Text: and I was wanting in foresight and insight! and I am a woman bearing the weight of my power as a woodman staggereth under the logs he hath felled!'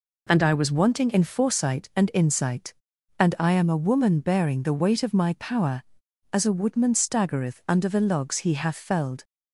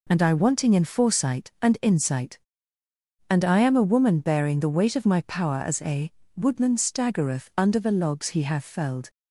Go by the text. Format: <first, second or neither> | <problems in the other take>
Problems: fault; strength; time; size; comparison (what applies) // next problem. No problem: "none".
first | skips "was"; at 0.3 s // pauses between "a" and "woodman"; slight; at 6.0 s; 0.28 s long